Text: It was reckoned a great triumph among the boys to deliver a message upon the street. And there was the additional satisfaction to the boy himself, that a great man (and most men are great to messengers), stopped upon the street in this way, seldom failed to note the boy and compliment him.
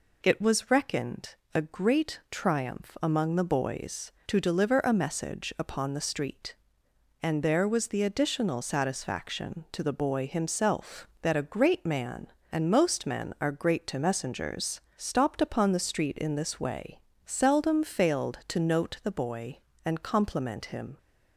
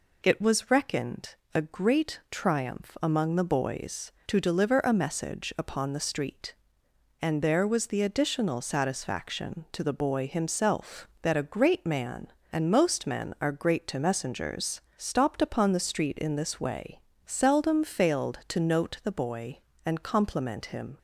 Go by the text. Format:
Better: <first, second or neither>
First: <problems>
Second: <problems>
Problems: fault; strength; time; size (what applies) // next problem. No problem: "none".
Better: neither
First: pauses between "reckoned" and "a"; slight; at 1.3 s; 0.20 s long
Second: pauses between "reckoned" and "a"; slight; at 1.3 s; 0.20 s long